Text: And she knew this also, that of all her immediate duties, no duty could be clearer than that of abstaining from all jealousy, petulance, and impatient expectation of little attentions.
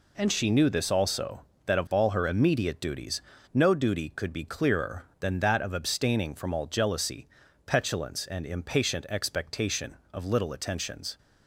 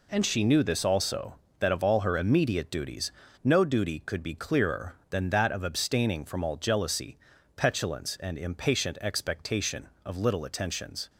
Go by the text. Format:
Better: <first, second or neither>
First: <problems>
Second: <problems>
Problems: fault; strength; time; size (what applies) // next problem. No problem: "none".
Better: neither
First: none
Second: none